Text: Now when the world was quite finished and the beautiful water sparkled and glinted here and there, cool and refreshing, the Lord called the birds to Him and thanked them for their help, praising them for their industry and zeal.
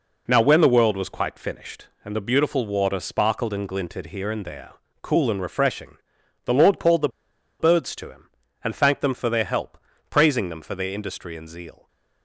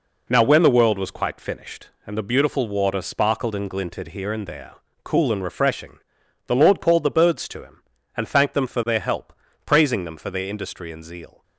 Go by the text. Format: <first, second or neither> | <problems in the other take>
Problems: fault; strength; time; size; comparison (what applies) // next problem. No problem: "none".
second | pauses between "the" and "birds"; noticeable; at 7.0 s; 0.51 s long